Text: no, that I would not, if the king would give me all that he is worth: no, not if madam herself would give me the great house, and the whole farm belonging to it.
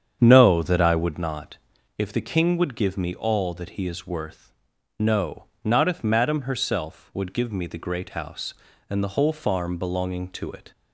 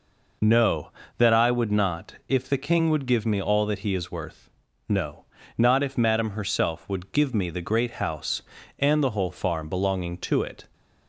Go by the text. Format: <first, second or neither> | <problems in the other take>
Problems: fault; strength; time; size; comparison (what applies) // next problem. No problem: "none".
second | starts louder than the rest; strong; until 1.2 s; 8 dB